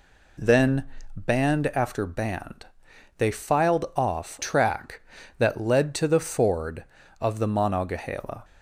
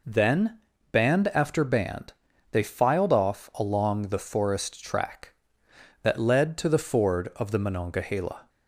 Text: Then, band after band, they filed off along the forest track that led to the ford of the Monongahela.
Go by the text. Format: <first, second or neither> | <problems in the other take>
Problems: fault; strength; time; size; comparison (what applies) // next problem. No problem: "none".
second | skips "along the forest"; at 4.4 s